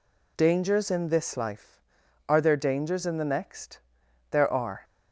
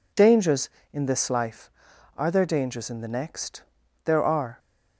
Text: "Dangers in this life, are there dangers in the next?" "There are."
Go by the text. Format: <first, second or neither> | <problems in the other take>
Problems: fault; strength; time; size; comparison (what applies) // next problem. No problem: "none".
neither | none